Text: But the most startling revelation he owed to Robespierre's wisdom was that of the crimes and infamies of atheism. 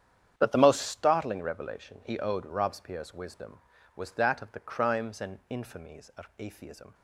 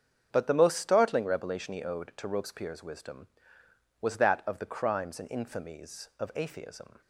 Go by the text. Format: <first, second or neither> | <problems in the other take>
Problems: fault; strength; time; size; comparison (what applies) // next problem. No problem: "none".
second | starts louder than the rest; strong; until 1.3 s; 9 dB; strong in the second // skips "to"; at 2.4 s